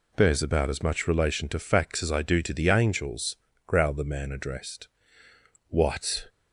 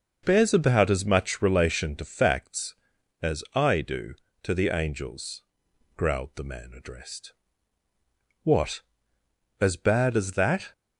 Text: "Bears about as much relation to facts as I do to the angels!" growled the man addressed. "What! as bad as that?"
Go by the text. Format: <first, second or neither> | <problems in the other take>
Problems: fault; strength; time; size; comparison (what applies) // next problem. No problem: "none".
second | stops before "as bad as that"; at 6.2 s